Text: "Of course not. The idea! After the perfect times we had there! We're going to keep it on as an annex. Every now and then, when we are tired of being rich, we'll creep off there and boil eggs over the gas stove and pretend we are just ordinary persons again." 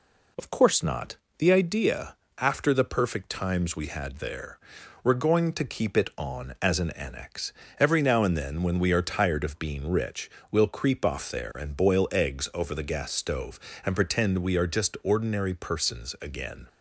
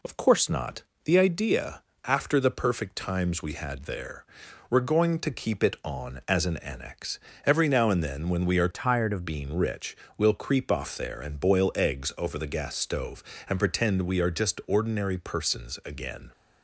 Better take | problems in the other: first | changes voice from "tired" to "of"; from 8.7 to 9.2 s; 0.5 s long

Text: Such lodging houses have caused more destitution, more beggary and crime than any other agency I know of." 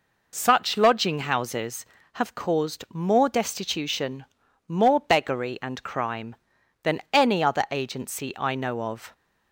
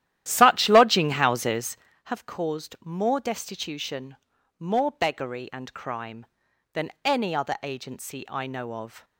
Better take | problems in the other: first | starts louder than the rest; strong; until 1.8 s; 12.5 dB

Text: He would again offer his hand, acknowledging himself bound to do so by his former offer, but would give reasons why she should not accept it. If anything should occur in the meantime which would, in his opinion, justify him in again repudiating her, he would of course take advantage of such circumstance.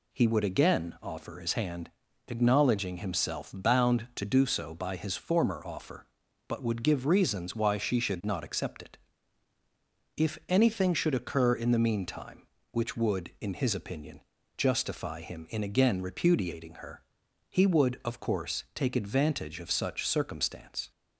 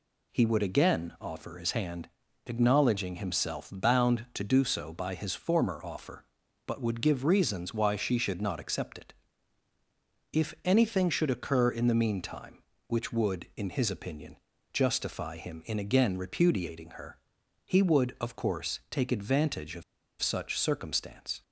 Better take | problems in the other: first | pauses between "of" and "such"; at 19.8 s; 0.38 s long

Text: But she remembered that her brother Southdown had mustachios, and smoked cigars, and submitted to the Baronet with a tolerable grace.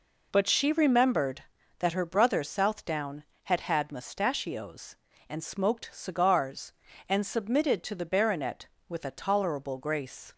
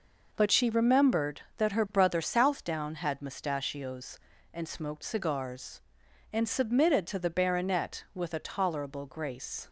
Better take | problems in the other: second | says "had" twice; at 3.5 s

